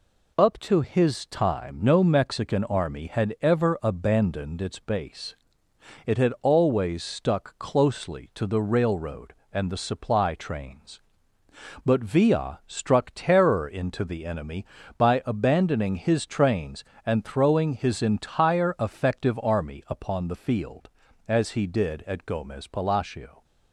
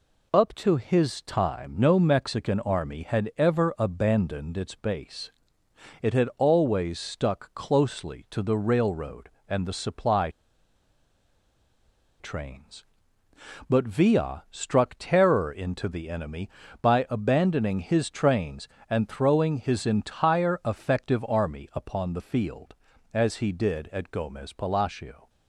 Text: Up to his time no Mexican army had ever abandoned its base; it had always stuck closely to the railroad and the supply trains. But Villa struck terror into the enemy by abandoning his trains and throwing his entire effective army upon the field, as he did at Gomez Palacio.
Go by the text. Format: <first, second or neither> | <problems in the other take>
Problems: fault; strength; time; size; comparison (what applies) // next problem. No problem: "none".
first | pauses between "supply" and "trains"; strong; at 10.2 s; 1.9 s long